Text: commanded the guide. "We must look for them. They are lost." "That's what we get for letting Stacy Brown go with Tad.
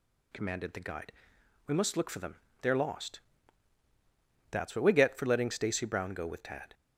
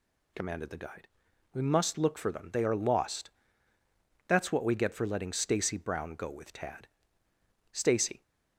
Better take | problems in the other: first | goes on to say "Stacy"; from 7.7 s on; 0.50 s long

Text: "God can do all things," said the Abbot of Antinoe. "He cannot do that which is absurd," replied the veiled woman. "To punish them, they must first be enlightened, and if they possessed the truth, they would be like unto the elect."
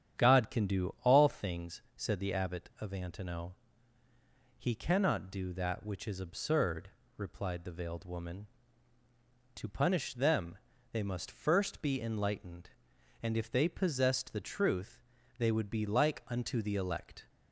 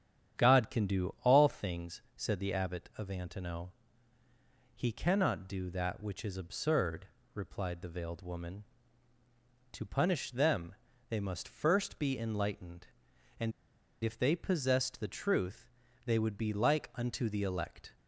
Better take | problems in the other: first | starts louder than the rest; strong; until 1.4 s; 9.5 dB; strong in the first // pauses between "and" and "if"; noticeable; at 13.5 s; 0.52 s long

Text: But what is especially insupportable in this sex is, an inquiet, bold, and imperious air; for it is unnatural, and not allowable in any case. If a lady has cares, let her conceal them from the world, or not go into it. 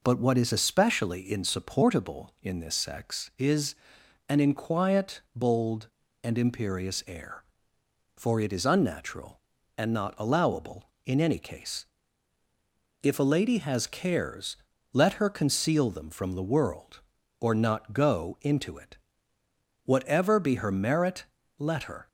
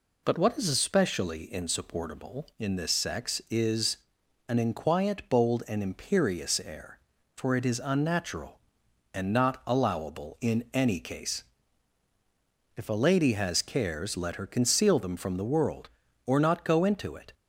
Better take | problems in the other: second | goes on to say "Whatever be her merit let her"; strong; from 19.8 s on; 2.2 s long

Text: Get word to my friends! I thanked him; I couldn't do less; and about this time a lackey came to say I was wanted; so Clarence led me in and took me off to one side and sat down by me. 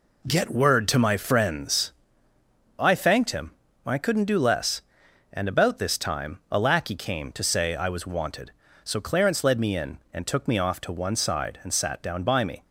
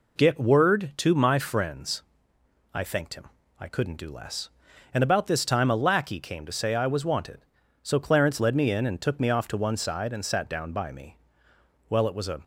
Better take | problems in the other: first | goes on to say "Well it was a"; from 11.8 s on; 0.54 s long

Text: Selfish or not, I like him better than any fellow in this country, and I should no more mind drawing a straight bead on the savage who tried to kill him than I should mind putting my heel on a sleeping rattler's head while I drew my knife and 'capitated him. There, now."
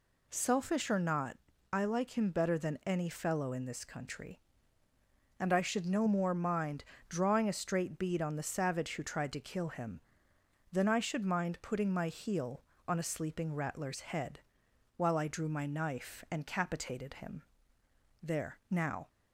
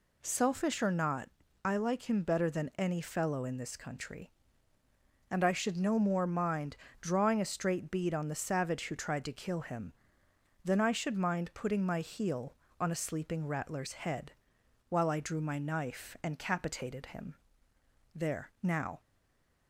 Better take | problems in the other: first | pauses between "mind" and "drawing"; slight; at 6.7 s; 0.24 s long; slight in the first // pauses between "head" and "while"; noticeable; at 14.3 s; 0.58 s long; noticeable in the first // stays silent after the last word; slight; from 18.9 s on; 0.7 s long

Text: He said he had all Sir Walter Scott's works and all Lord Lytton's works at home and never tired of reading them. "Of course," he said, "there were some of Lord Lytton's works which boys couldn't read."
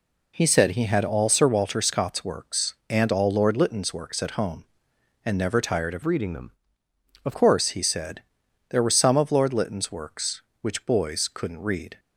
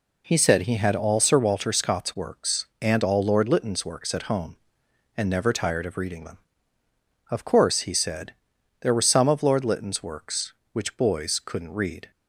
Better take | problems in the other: second | changes voice from "reading" to "Of"; from 6.0 to 7.3 s; 1.3 s long

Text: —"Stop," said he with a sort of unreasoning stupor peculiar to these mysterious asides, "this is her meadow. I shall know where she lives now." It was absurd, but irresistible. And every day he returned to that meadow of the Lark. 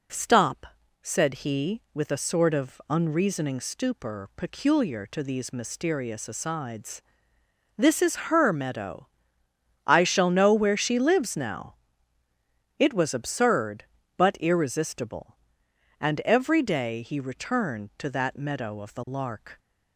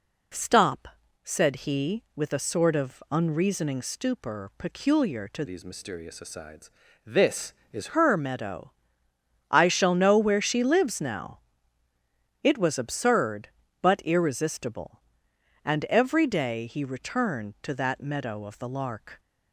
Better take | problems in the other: first | changes voice from "these" to "is"; from 5.4 to 7.9 s; 2.5 s long

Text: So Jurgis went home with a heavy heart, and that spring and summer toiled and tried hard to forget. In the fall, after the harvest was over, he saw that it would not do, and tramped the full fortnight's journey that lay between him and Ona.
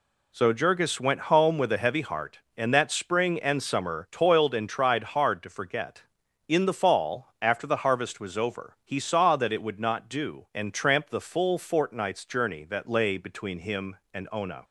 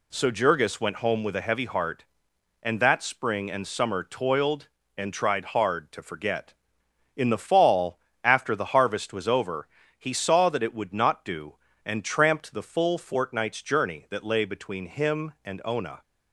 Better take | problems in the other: neither | none

